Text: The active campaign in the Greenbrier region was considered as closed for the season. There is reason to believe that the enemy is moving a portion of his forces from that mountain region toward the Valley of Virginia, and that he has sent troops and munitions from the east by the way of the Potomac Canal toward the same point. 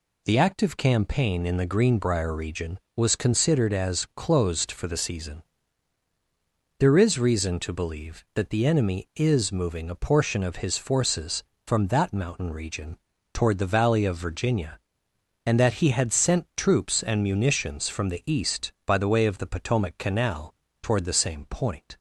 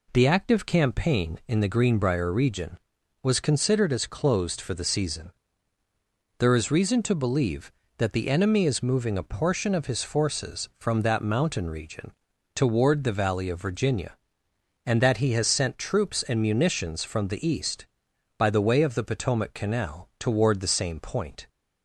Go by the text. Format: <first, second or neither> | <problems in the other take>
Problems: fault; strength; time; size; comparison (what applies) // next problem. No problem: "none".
second | pauses between "region" and "toward"; slight; at 12.9 s; 0.36 s long; also in the second // says "had" for "has"; at 15.9 s // pauses between "Canal" and "toward"; slight; at 20.5 s; 0.30 s long